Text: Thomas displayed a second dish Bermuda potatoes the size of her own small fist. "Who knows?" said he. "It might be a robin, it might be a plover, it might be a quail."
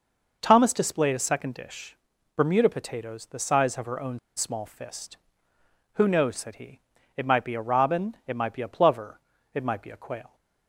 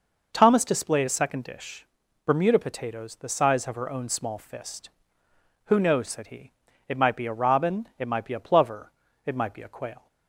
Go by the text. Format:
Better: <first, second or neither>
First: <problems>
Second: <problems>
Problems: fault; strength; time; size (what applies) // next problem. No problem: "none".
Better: second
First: pauses between "dish" and "Bermuda"; at 1.9 s; 0.40 s long // pauses between "own" and "small"; slight; at 4.1 s; 0.17 s long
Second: pauses between "dish" and "Bermuda"; at 1.8 s; 0.40 s long